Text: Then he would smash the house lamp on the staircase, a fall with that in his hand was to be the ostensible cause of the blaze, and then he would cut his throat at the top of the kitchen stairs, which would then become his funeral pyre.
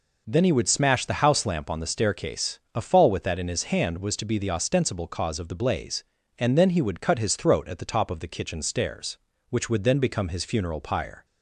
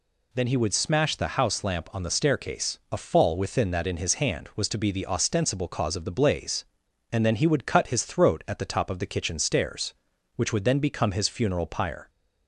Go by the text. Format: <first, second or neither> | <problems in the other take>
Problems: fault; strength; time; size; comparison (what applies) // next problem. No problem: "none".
first | says "within" for "with"; at 3.3 s